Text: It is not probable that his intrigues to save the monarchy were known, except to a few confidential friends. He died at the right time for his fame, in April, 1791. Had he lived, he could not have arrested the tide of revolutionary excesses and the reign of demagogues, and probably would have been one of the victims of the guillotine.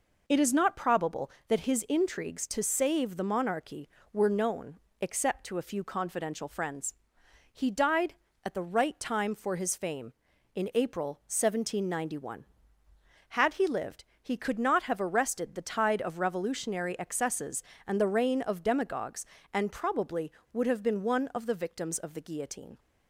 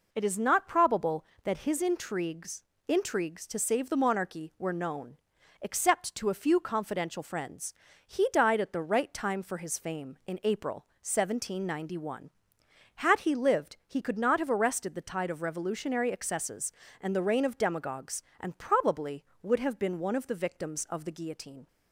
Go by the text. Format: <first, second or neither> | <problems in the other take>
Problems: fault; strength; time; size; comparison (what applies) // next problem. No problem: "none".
first | says "intrigues" twice; at 2.8 s